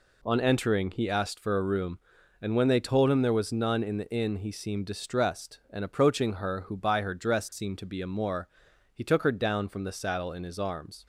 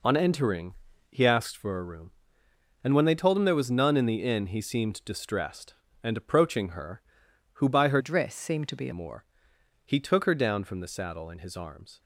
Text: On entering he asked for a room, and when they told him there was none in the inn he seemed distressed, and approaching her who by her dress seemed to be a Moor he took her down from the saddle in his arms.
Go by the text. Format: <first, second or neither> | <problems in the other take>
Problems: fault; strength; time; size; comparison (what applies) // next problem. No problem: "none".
first | pauses between "entering" and "he"; slight; at 0.7 s; 0.36 s long // changes voice from "dress" to "a"; from 7.9 to 8.9 s; 1.0 s long // pauses between "Moor" and "he"; noticeable; at 9.2 s; 0.62 s long; also in the first